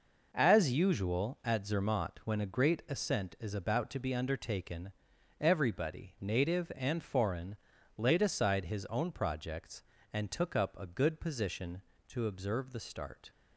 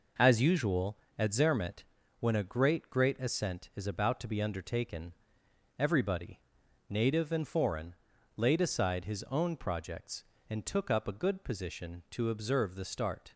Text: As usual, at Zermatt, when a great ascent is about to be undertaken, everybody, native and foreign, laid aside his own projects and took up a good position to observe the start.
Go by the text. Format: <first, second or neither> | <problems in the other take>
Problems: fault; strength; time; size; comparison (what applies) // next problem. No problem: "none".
first | says "great" twice; at 2.8 s